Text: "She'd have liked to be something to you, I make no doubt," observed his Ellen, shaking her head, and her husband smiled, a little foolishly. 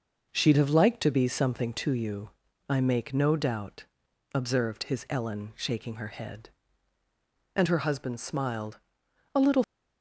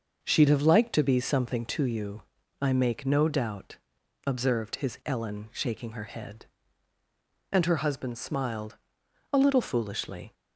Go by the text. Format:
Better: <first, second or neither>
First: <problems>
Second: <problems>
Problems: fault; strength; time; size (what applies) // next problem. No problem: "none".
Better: second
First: stops before "foolishly"; at 9.6 s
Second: none